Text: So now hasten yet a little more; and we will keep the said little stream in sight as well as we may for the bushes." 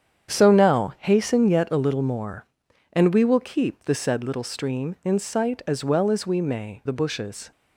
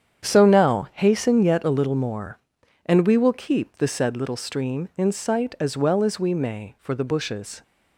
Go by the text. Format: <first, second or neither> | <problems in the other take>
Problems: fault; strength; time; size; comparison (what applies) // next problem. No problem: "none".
second | starts louder than the rest; strong; until 1.3 s; 8 dB; strong in the second // skips "for"; at 6.8 s